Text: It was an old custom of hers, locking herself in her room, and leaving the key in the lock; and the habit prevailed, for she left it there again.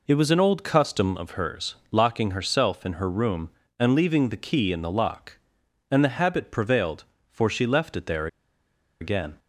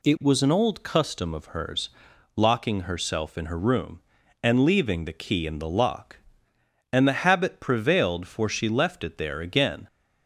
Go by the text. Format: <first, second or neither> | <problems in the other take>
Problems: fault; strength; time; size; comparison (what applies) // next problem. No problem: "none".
second | pauses between "there" and "again"; noticeable; at 8.2 s; 0.73 s long